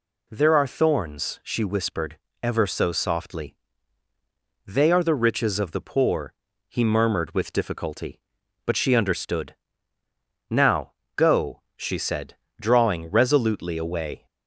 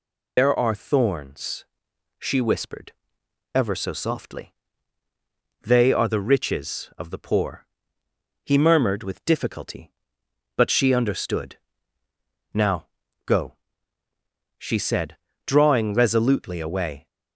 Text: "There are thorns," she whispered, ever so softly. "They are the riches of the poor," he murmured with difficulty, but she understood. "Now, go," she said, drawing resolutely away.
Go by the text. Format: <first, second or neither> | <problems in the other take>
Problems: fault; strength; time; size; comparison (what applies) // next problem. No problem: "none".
first | loses the start of "There"; at 0.3 s; 110 ms